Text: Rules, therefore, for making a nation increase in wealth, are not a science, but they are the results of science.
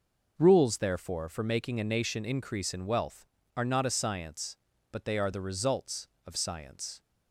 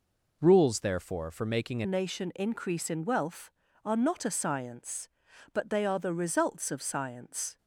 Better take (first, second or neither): first